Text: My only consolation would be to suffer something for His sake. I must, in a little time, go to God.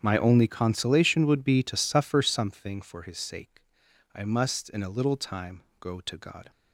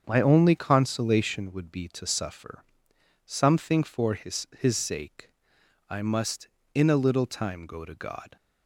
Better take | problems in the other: first | starts louder than the rest; until 1.0 s; 7 dB; strong in the first // pauses between "suffer" and "something"; noticeable; at 2.6 s; 0.60 s long // says "His" twice; at 4.5 s

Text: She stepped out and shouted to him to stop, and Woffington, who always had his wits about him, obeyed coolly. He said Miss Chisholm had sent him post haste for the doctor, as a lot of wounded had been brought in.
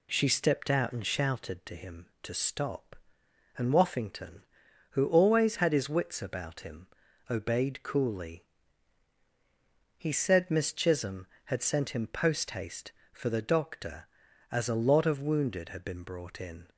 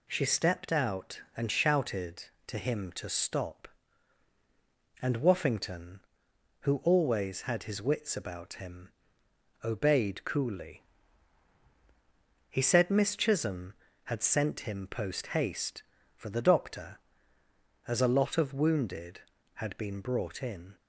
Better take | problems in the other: neither | none

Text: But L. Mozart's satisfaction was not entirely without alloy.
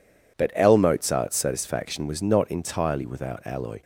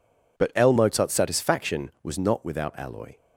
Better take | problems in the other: first | skips "entirely"; at 2.4 s

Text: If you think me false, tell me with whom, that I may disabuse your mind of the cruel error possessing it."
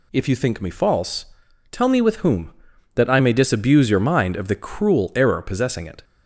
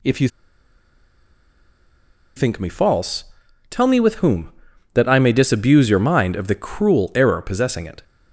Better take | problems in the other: first | pauses between "you" and "think"; strong; at 0.2 s; 2.0 s long

